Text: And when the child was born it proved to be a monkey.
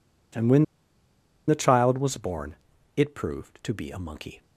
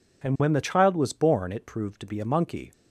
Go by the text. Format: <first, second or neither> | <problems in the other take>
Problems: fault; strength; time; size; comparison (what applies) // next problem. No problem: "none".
second | pauses between "when" and "the"; noticeable; at 0.6 s; 0.84 s long // pauses between "born" and "it"; at 2.5 s; 0.38 s long